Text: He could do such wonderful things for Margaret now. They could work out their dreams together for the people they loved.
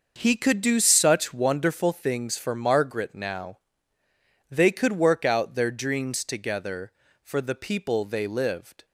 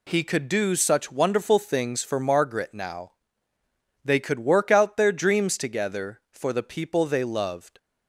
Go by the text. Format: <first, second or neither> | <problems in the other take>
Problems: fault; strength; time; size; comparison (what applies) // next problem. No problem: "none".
second | starts louder than the rest; noticeable; until 1.1 s; 6 dB // says "lived" for "loved"; at 8.2 s